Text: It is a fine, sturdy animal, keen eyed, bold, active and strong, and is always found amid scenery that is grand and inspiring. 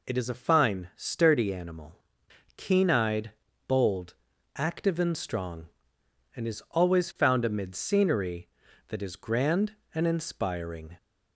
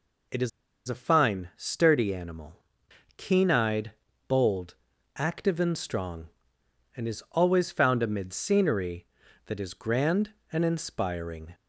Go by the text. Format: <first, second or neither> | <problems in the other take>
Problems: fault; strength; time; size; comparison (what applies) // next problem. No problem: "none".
first | pauses between "is" and "a"; at 0.4 s; 0.38 s long